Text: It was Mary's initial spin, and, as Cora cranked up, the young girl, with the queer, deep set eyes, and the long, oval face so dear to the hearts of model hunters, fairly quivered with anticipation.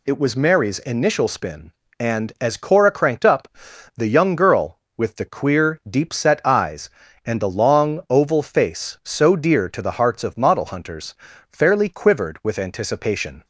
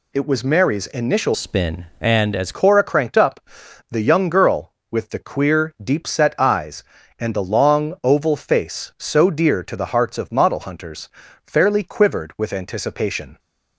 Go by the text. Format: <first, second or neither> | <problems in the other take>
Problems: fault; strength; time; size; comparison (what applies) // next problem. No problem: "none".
first | changes voice from "spin" to "as"; from 1.3 to 2.5 s; 1.2 s long